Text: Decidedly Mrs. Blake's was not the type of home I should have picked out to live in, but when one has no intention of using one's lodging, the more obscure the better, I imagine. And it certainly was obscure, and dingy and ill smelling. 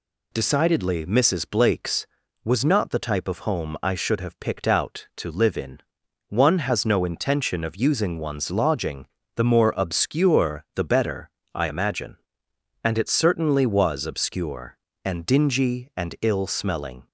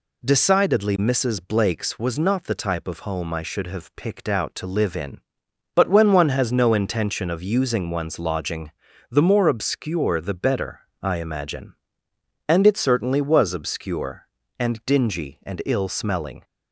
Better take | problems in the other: second | skips "but when"; at 6.0 s

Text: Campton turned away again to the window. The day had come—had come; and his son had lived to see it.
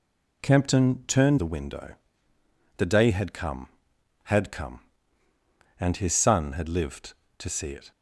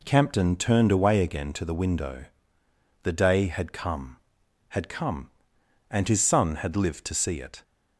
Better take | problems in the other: second | skips "away again to"; at 1.3 s

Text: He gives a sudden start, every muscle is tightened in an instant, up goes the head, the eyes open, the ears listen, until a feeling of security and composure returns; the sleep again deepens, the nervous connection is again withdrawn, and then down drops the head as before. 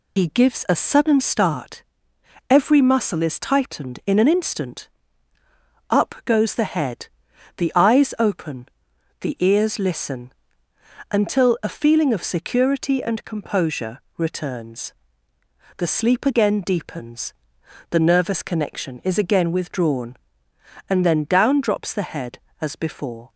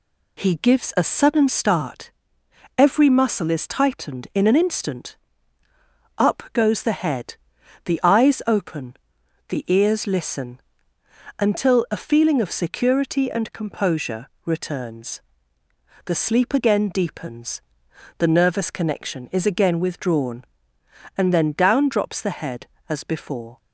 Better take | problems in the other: second | loses the start of "He"; at 0.1 s; 70 ms // pauses between "composure" and "returns"; slight; at 14.0 s; 0.18 s long; slight in the second

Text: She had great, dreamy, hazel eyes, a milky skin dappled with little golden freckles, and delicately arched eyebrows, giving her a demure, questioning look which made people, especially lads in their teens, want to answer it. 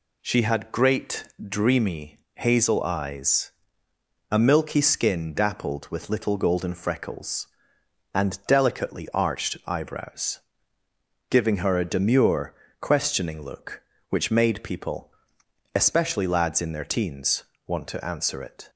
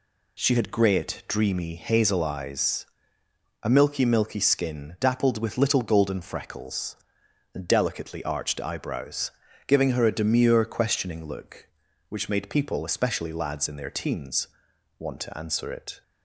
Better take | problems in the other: first | says "milky" twice; at 4.0 s

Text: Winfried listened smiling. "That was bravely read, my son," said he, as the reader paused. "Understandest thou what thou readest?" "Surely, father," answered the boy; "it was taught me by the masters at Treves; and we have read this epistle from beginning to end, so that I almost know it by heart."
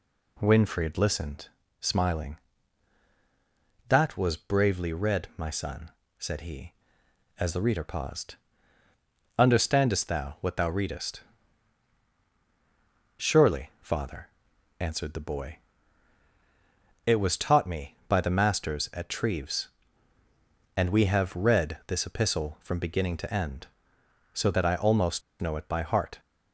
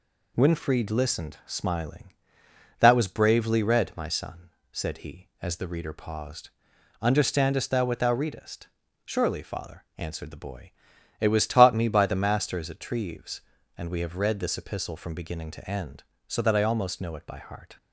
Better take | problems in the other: second | pauses between "listened" and "smiling"; slight; at 1.4 s; 0.32 s long // pauses between "almost" and "know"; slight; at 25.2 s; 0.20 s long

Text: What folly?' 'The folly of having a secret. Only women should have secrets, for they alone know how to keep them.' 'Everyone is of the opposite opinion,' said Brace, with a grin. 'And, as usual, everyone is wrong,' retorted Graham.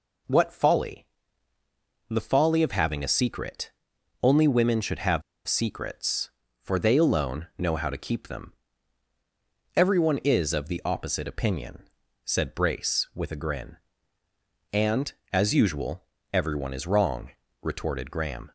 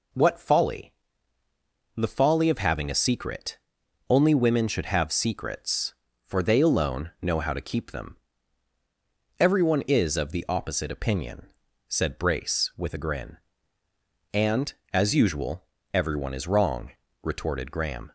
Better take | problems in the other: second | pauses between "have" and "secrets"; slight; at 5.2 s; 0.25 s long

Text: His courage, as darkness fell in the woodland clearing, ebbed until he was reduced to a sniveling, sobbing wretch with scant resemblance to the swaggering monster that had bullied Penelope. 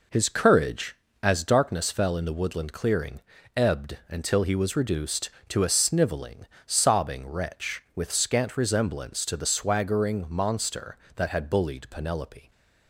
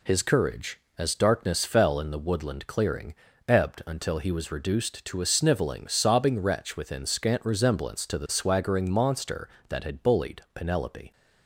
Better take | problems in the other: first | says "within" for "with"; at 6.7 s

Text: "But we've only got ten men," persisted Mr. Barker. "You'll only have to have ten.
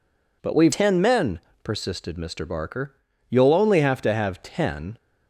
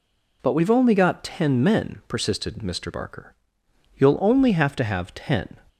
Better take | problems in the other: second | skips "only got"; at 0.7 s

